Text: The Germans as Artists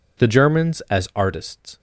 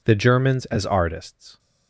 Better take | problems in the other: neither | none

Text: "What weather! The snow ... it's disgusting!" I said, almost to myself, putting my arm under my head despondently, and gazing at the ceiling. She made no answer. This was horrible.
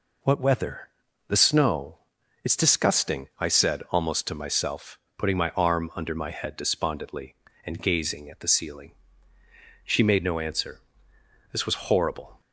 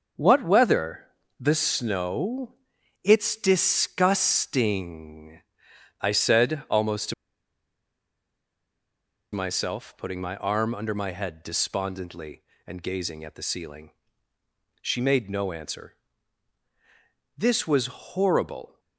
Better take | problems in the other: first | pauses between "to" and "myself"; strong; at 7.1 s; 2.1 s long

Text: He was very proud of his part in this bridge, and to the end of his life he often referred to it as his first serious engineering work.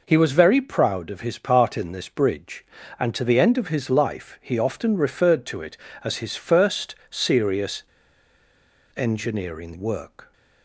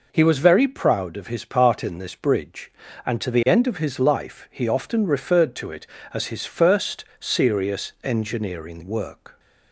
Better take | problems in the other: second | pauses between "first" and "serious"; slight; at 6.9 s; 0.16 s long; slight in the second // pauses between "serious" and "engineering"; at 7.8 s; 1.1 s long

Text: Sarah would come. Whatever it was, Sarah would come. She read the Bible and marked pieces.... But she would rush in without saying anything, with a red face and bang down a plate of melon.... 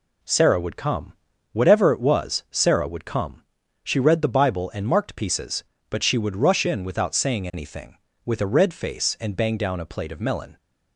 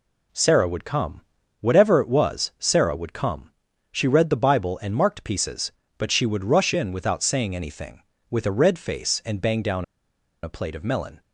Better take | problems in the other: first | pauses between "down" and "a"; noticeable; at 9.8 s; 0.59 s long

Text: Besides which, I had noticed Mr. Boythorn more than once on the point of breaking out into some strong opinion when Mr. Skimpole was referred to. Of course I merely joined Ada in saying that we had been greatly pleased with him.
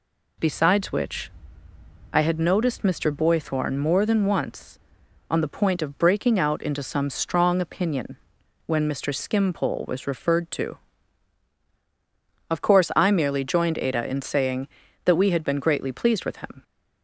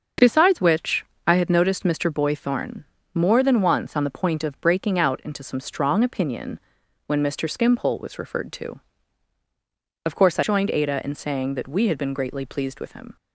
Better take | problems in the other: first | starts louder than the rest; until 1.3 s; 6.5 dB // pauses between "Boythorn" and "more"; slight; at 2.8 s; 0.30 s long // pauses between "opinion" and "when"; noticeable; at 6.5 s; 0.48 s long; noticeable in the first // skips "merely"; at 10.4 s

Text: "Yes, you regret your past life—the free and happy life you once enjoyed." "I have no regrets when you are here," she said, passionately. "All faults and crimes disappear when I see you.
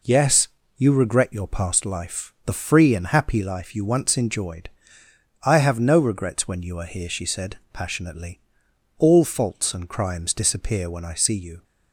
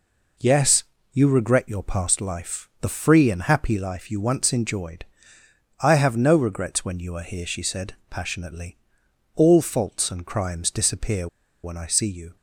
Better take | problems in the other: first | pauses between "disappear" and "when"; at 11.2 s; 0.36 s long

